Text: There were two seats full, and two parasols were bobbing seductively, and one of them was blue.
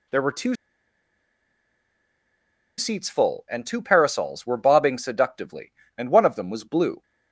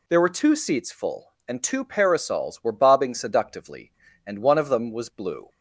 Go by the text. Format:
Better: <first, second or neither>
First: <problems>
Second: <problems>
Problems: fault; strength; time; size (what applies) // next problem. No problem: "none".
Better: second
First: pauses between "two" and "seats"; strong; at 0.5 s; 2.2 s long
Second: none